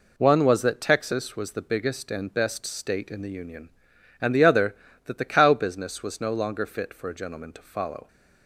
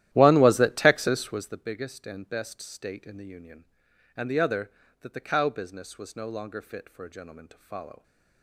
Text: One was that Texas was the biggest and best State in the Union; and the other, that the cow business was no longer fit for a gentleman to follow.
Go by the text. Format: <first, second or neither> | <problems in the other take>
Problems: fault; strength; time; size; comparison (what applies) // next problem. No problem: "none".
first | starts louder than the rest; strong; until 1.6 s; 13.5 dB